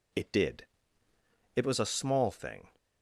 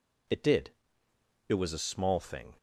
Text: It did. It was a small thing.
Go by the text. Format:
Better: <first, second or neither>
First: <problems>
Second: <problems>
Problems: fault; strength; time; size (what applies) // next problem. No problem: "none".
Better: neither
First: none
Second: none